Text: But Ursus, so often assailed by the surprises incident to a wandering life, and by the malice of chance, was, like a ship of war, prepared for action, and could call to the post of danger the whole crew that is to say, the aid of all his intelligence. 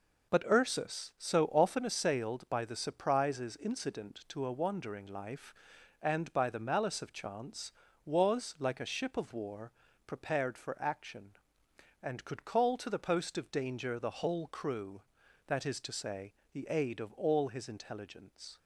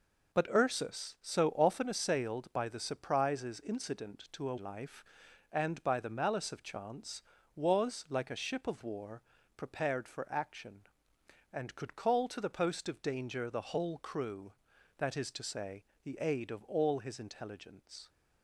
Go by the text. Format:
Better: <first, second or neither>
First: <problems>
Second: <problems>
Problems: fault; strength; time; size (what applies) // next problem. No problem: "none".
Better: first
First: none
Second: skips "wandering"; at 4.5 s